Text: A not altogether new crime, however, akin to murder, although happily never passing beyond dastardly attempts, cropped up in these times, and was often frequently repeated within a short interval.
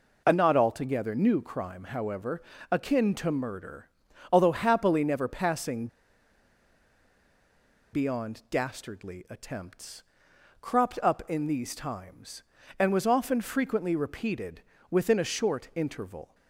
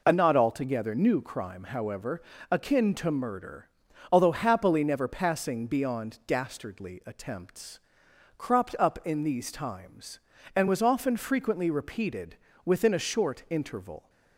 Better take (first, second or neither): second